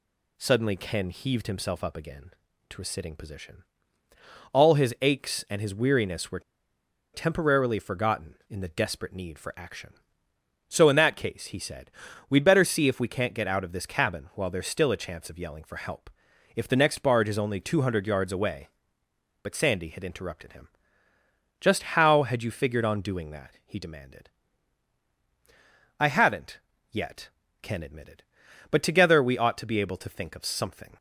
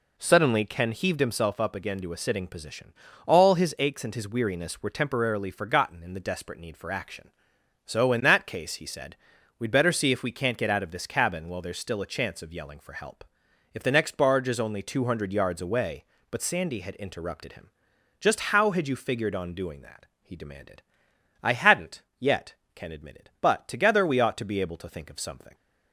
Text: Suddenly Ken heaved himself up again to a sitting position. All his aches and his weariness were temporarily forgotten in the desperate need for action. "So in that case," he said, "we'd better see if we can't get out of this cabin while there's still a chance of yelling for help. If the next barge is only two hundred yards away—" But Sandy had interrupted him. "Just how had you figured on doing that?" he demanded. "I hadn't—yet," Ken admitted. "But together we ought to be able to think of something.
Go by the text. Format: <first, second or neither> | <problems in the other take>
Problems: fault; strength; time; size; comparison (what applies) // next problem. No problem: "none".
second | pauses between "were" and "temporarily"; noticeable; at 6.3 s; 0.73 s long